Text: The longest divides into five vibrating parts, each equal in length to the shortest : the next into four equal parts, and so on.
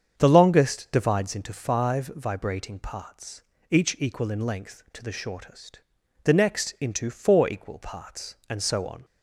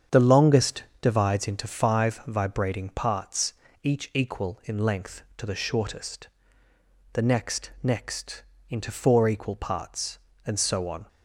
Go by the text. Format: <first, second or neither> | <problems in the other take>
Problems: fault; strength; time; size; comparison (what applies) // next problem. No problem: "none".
first | starts louder than the rest; strong; until 1.2 s; 8 dB; strong in the first // pauses between "longest" and "divides"; slight; at 0.8 s; 0.16 s long // says "next" twice; at 7.8 s